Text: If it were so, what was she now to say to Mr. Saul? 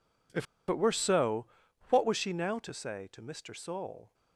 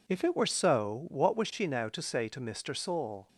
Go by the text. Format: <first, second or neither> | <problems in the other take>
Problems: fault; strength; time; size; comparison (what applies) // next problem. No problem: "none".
second | pauses between "If" and "it"; slight; at 0.4 s; 0.24 s long